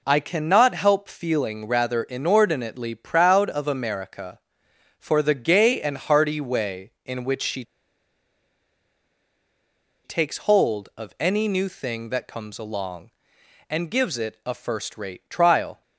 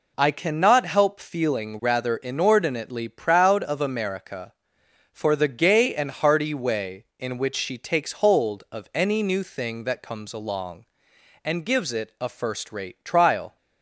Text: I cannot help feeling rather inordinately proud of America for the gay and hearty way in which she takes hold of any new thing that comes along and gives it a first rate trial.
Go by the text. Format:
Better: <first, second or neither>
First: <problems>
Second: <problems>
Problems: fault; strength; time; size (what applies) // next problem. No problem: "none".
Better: second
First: pauses between "she" and "takes"; strong; at 7.6 s; 2.4 s long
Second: none